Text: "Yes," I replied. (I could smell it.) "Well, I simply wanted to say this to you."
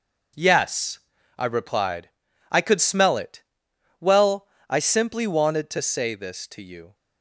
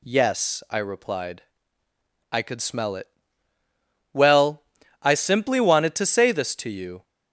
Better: second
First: gets quieter; strong; throughout; 9 dB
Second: none

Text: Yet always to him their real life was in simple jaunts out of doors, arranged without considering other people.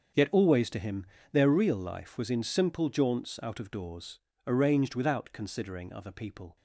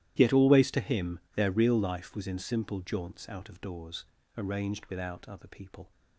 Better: first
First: starts louder than the rest; until 1.4 s; 6.5 dB // pauses between "him" and "their"; slight; at 1.0 s; 0.26 s long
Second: starts louder than the rest; strong; until 1.1 s; 13 dB // pauses between "him" and "their"; slight; at 1.1 s; 0.16 s long // skips "considering"; at 5.2 s

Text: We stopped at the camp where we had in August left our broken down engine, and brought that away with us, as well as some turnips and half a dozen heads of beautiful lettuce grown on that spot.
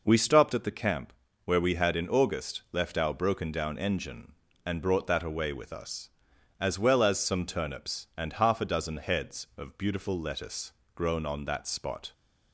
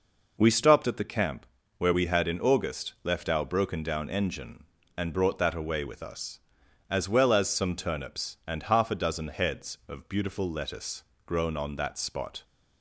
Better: neither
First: pauses between "camp" and "where"; slight; at 1.1 s; 0.32 s long // pauses between "lettuce" and "grown"; slight; at 10.7 s; 0.22 s long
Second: pauses between "camp" and "where"; slight; at 1.4 s; 0.32 s long // pauses between "lettuce" and "grown"; slight; at 11.0 s; 0.22 s long

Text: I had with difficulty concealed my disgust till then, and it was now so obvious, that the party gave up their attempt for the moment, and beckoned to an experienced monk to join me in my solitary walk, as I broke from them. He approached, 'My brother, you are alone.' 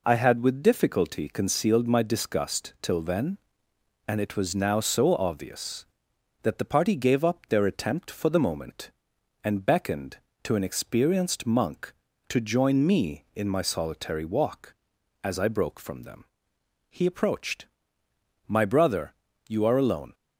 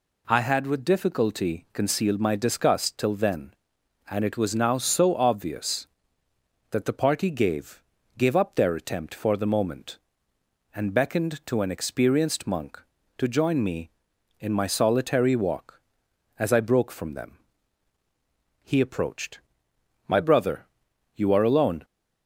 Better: first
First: none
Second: says "gave" twice; at 8.1 s

